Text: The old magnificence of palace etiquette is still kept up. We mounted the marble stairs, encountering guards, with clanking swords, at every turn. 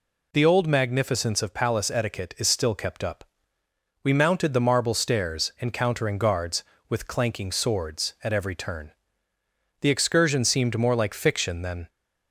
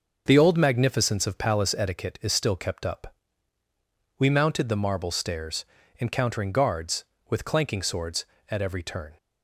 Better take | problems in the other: second | goes on to say "The excursion seemed more like fiction than"; strong; from 9.8 s on; 2.0 s long

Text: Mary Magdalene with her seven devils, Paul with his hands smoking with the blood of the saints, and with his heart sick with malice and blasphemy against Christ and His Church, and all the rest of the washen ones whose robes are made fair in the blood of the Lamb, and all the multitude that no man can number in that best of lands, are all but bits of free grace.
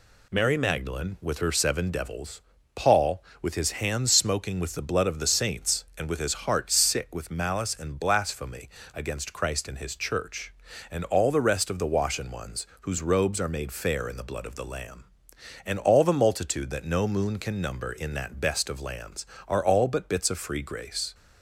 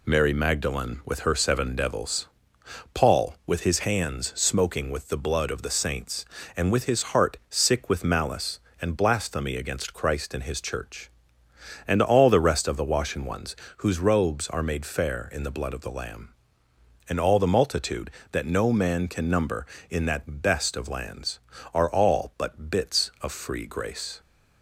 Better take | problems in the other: second | pauses between "blasphemy" and "against"; slight; at 8.6 s; 0.26 s long // pauses between "ones" and "whose"; slight; at 12.6 s; 0.16 s long; slight in the second // says "moon" for "man"; at 17.0 s

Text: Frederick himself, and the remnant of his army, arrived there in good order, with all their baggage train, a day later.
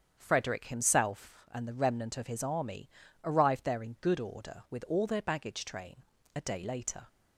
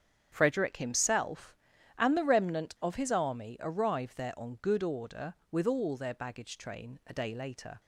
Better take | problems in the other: first | starts louder than the rest; strong; until 1.3 s; 8.5 dB; strong in the first // says "on" for "in"; at 4.3 s

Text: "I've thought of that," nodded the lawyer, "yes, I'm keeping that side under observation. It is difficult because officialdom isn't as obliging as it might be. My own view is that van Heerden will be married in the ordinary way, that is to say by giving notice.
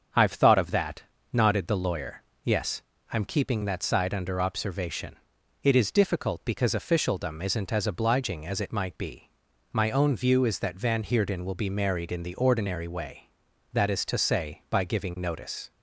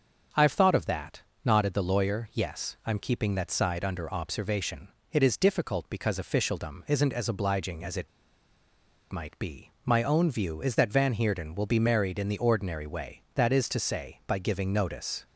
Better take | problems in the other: first | starts louder than the rest; until 1.5 s; 6.5 dB; also in the first // pauses between "it" and "might"; at 8.0 s; 1.0 s long

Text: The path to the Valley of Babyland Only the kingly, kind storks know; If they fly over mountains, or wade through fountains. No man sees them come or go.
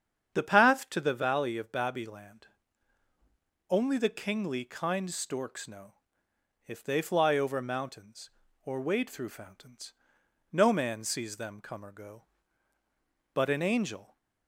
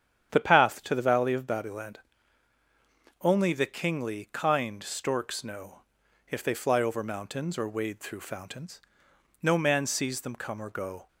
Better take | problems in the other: second | starts louder than the rest; strong; until 1.3 s; 8 dB; strong in the second // pauses between "Babyland" and "Only"; at 2.4 s; 1.2 s long; also in the second // goes on to say "But an angel"; noticeable; from 13.3 s on; 0.84 s long

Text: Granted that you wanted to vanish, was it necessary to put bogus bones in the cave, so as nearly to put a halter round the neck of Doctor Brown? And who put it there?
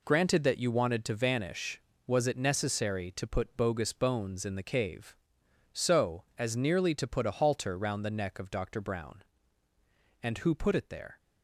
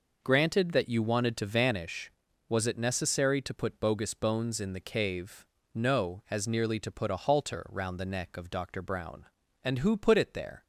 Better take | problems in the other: first | says "no" for "so"; at 5.7 s

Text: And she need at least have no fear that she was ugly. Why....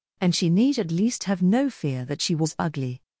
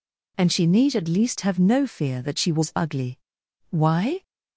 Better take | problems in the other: second | stops before "Why"; at 3.0 s

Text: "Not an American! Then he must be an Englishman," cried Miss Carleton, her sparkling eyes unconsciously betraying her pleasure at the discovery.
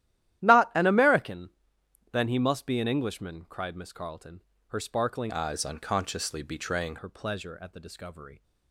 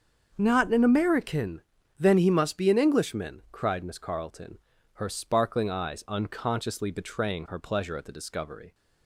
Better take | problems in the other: second | starts louder than the rest; strong; until 1.4 s; 13 dB; also in the second // changes voice from "eyes" to "betraying"; from 5.3 to 6.9 s; 1.6 s long

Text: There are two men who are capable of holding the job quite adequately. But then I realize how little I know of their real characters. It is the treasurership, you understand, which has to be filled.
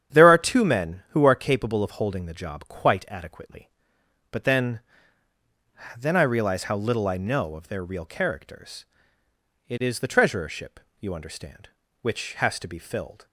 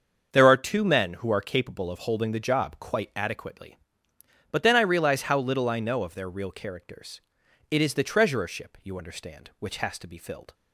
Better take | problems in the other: second | starts louder than the rest; strong; until 1.2 s; 9 dB; also in the second // says "then" twice; at 5.9 s

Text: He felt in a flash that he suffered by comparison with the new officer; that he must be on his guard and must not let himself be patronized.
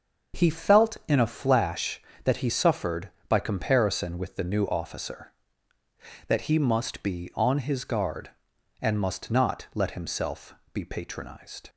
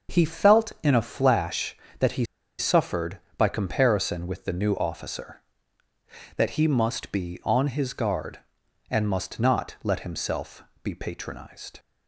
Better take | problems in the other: first | starts louder than the rest; until 1.1 s; 6.5 dB; also in the first // pauses between "he" and "suffered"; slight; at 2.2 s; 0.34 s long // pauses between "himself" and "be"; slight; at 10.6 s; 0.18 s long; slight in the first

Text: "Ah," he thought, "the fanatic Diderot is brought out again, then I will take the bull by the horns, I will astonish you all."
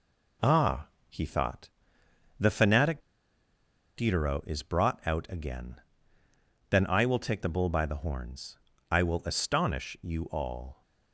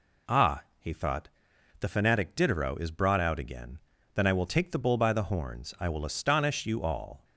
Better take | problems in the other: second | pauses between "fanatic" and "Diderot"; noticeable; at 3.0 s; 0.96 s long

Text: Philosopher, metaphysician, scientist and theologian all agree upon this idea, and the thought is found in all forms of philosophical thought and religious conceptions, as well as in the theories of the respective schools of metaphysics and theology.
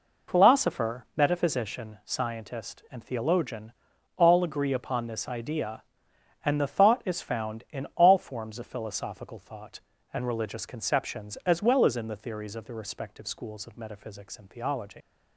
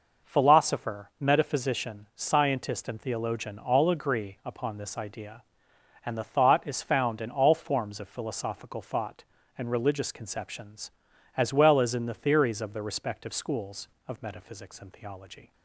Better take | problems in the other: second | pauses between "theologian" and "all"; at 3.7 s; 0.44 s long // leaves "theology" unfinished; at 15.0 s; 85 ms

